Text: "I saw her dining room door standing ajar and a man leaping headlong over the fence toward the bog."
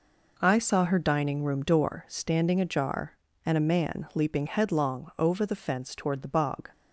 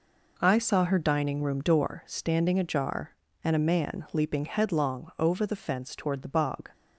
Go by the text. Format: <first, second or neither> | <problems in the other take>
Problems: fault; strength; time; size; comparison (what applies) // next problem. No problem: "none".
neither | none